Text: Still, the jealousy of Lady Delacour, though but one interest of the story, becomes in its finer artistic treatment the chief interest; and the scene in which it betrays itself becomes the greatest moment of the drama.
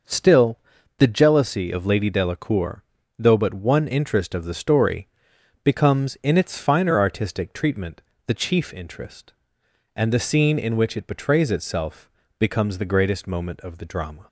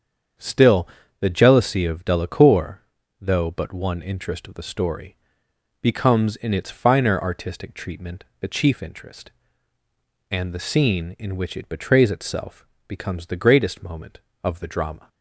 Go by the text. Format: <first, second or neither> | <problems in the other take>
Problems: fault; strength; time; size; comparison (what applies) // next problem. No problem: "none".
first | starts louder than the rest; strong; until 1.6 s; 7.5 dB; also in the first // skips "Lady"; at 2.0 s // pauses between "treatment" and "the"; slight; at 8.2 s; 0.16 s long; slight in the first // pauses between "itself" and "becomes"; slight; at 12.6 s; 0.20 s long; slight in the first